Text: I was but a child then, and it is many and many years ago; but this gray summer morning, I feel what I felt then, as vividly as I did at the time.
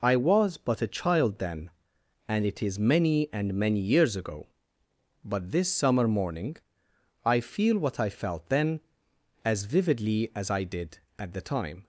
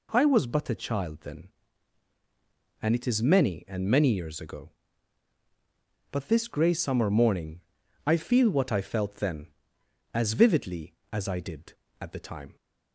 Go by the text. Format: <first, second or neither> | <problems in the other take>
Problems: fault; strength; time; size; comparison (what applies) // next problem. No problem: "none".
second | skips "gray"; at 5.7 s